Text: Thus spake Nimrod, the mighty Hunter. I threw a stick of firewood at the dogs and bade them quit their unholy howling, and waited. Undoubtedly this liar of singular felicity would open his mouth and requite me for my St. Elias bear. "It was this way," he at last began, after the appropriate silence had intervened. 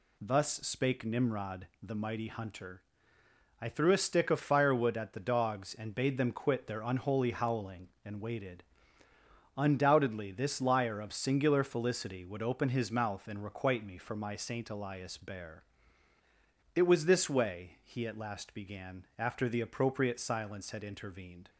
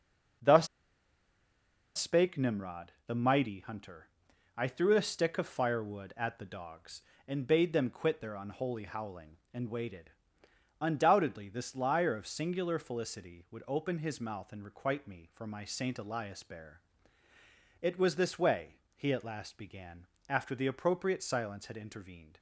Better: first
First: none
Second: starts louder than the rest; noticeable; until 2.7 s; 6 dB // pauses between "Thus" and "spake"; strong; at 0.6 s; 1.3 s long

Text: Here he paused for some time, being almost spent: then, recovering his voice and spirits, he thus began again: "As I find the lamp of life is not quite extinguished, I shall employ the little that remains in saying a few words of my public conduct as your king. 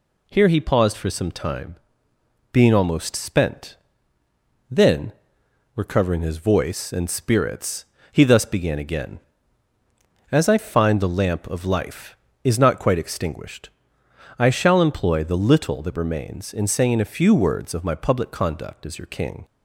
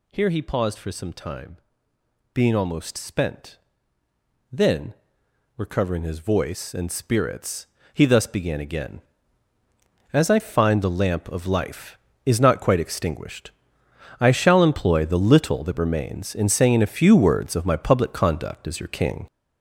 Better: first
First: none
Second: gets louder; strong; throughout; 7.5 dB

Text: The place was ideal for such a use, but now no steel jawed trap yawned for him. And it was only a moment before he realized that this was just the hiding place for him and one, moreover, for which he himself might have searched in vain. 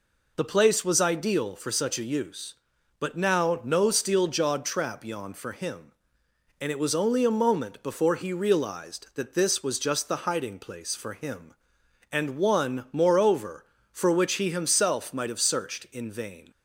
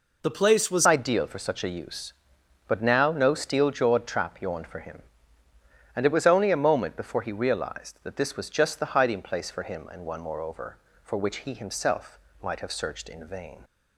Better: first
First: none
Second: changes voice at "ideal"; from 0.8 s on; 12.8 s long // pauses between "himself" and "might"; slight; at 12.1 s; 0.24 s long

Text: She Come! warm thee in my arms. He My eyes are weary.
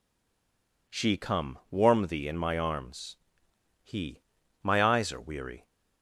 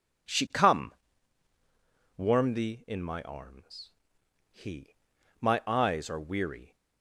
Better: second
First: stays silent before the first word; slight; until 0.8 s; 0.8 s long // pauses between "He" and "My"; at 4.2 s; 0.40 s long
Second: pauses between "He" and "My"; noticeable; at 4.9 s; 0.48 s long

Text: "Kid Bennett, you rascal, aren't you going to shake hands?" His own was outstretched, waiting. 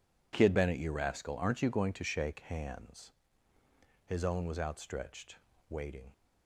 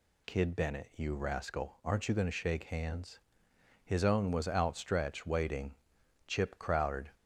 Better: first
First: none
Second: goes on to say "Chip crowded"; noticeable; from 6.2 s on; 0.85 s long

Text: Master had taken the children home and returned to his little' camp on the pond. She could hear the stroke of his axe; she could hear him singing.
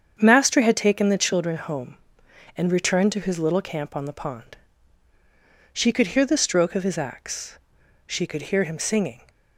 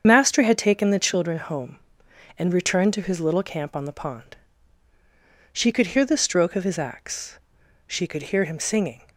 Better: first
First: starts louder than the rest; strong; until 1.2 s; 7.5 dB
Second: loses the start of "Master"; at 0.0 s; 50 ms // starts louder than the rest; strong; until 1.0 s; 7.5 dB

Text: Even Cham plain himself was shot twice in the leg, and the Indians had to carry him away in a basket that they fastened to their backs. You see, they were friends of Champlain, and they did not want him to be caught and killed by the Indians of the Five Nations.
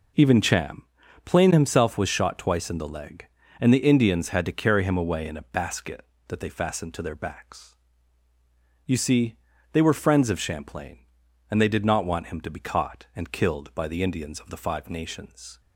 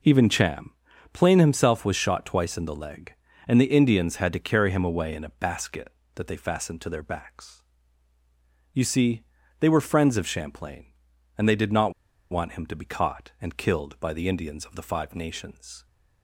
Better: first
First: pauses between "Cham" and "plain"; at 0.8 s; 0.42 s long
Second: pauses between "Cham" and "plain"; at 0.7 s; 0.42 s long // pauses between "not" and "want"; at 11.9 s; 0.39 s long

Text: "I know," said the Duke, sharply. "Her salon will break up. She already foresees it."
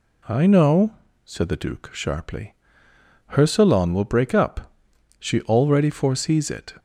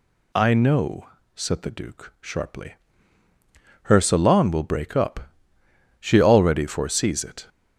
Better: neither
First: none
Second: none

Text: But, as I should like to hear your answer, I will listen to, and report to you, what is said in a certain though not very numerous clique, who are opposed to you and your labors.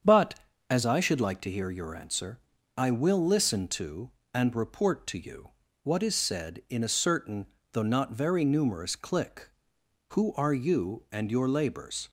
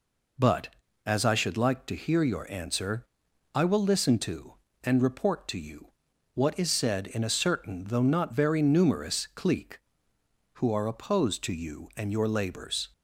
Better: second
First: starts louder than the rest; strong; until 1.4 s; 7.5 dB // pauses between "certain" and "though"; slight; at 7.4 s; 0.26 s long // skips "opposed to"; at 10.5 s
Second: none

